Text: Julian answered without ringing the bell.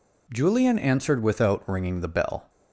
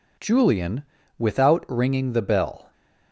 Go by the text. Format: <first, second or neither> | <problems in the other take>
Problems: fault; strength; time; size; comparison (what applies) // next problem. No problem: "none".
first | skips "answered"; at 1.0 s